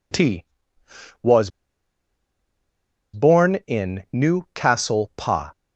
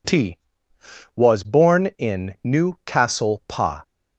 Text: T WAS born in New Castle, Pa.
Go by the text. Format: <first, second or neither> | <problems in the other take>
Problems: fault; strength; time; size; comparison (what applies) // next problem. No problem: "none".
second | pauses between "WAS" and "born"; strong; at 1.4 s; 1.6 s long